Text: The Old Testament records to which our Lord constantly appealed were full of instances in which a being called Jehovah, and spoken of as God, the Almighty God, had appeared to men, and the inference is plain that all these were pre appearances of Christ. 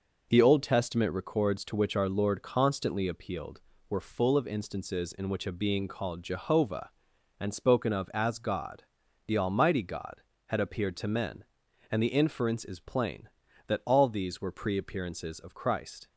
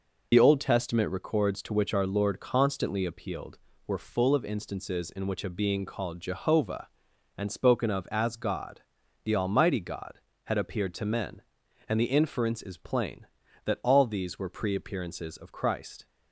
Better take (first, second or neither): first